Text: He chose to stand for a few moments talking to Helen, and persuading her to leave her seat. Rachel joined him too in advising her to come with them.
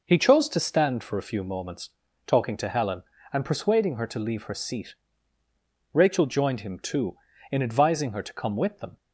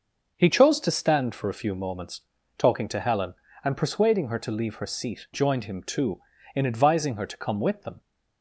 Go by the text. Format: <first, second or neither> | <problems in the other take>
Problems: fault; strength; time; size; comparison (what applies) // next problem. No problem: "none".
first | starts louder than the rest; noticeable; until 1.3 s; 6 dB // pauses between "moments" and "talking"; at 2.2 s; 0.38 s long; also in the first // skips "Rachel"; at 5.2 s